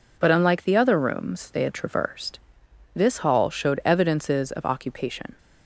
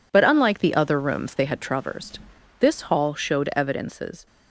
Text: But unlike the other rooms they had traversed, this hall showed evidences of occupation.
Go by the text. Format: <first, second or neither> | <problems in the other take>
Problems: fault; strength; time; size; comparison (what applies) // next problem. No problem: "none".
first | stops before "of occupation"; at 4.2 s